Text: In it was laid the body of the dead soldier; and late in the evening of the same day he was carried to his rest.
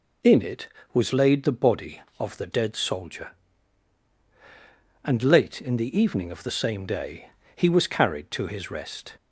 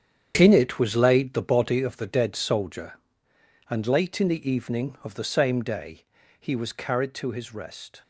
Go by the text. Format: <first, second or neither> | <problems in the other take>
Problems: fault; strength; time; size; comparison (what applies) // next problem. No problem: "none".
first | gets quieter; strong; throughout; 11 dB // pauses between "day" and "he"; slight; at 6.0 s; 0.36 s long; slight in the first